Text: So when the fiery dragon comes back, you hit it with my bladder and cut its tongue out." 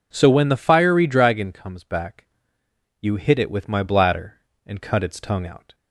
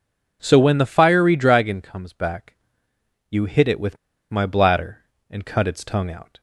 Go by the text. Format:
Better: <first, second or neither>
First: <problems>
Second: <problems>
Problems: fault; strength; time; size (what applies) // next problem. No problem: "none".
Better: first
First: none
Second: pauses between "with" and "my"; slight; at 3.9 s; 0.35 s long